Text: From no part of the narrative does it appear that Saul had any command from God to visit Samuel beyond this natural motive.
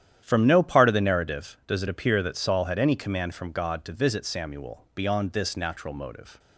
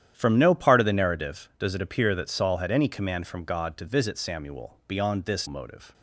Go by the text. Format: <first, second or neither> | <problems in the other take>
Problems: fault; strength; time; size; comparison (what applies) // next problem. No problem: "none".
first | starts louder than the rest; strong; until 1.1 s; 10.5 dB; strong in the first // skips "natural"; at 5.4 s